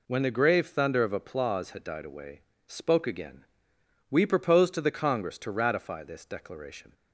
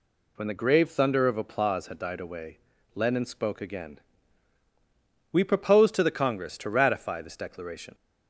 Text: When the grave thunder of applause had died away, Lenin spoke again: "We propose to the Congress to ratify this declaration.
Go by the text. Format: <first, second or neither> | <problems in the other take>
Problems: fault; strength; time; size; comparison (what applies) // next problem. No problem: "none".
second | skips "Lenin"; at 2.5 s